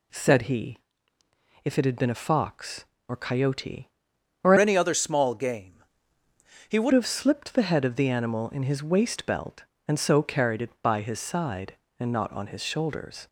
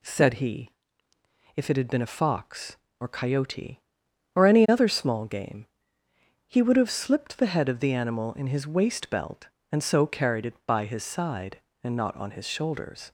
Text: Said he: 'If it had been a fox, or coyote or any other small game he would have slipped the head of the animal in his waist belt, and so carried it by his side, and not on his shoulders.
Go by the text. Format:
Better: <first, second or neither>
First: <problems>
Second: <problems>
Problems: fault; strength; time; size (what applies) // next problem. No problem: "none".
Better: second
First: changes voice from "any" to "would"; from 4.5 to 6.9 s; 2.4 s long // pauses between "game" and "he"; noticeable; at 5.8 s; 0.86 s long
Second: pauses between "game" and "he"; noticeable; at 5.6 s; 0.80 s long